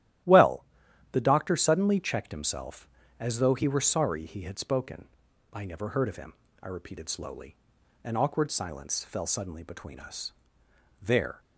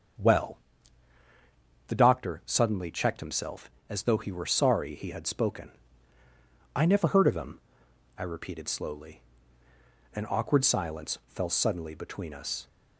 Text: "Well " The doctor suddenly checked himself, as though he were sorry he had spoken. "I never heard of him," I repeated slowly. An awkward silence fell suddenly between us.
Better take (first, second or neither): second